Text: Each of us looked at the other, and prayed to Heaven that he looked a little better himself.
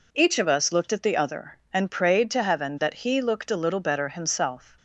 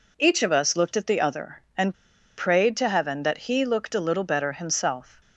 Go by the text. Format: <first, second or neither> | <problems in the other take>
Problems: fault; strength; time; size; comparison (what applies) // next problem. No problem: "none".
first | pauses between "and" and "prayed"; at 1.9 s; 0.44 s long